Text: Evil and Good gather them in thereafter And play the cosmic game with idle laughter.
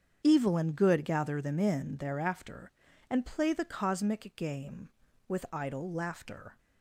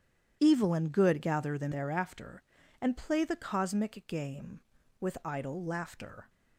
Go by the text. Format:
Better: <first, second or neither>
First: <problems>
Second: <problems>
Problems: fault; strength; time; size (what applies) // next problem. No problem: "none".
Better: first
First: starts louder than the rest; strong; until 1.2 s; 8 dB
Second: starts louder than the rest; strong; until 1.4 s; 10 dB // skips "in"; at 1.7 s